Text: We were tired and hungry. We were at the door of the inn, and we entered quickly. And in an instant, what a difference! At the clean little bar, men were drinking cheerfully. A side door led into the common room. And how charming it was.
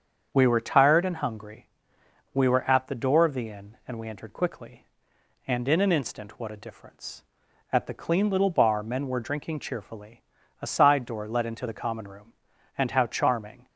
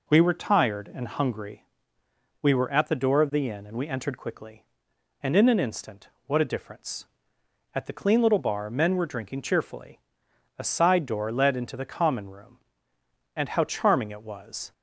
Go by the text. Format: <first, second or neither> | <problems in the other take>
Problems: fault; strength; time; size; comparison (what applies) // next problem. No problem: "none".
second | starts louder than the rest; strong; until 1.3 s; 7.5 dB // stops before "it was"; at 13.6 s